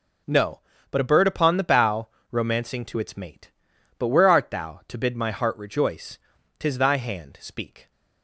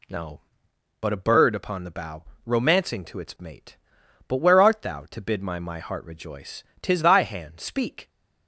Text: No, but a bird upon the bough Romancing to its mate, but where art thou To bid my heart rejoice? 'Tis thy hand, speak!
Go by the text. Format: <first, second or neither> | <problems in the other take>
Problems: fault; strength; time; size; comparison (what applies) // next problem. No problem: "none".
first | pauses between "bough" and "Romancing"; slight; at 2.2 s; 0.22 s long; slight in the first // says "my" twice; at 5.5 s